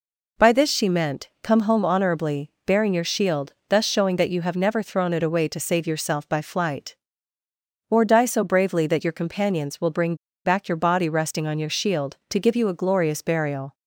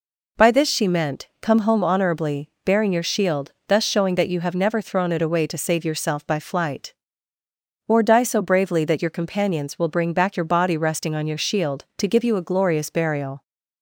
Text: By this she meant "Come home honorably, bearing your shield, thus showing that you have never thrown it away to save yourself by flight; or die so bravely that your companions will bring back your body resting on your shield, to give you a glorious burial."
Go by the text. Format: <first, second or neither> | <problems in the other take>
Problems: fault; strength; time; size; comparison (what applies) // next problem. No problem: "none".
second | pauses between "bring" and "back"; slight; at 10.1 s; 0.30 s long